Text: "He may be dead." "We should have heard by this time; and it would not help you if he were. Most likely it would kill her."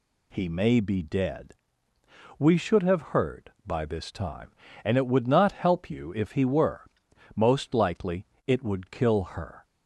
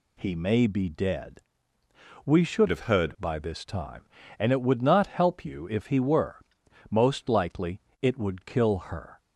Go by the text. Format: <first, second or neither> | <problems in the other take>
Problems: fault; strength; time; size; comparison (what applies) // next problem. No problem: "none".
first | changes voice from "have" to "heard"; from 2.6 to 3.1 s; 0.5 s long // pauses between "likely" and "it"; slight; at 7.8 s; 0.20 s long; slight in the first